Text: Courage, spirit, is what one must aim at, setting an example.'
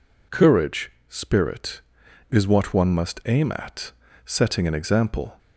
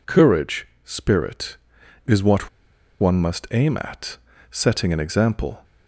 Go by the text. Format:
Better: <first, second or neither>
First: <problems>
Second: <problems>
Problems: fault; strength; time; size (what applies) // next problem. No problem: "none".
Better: first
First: none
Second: pauses between "what" and "one"; noticeable; at 2.4 s; 0.52 s long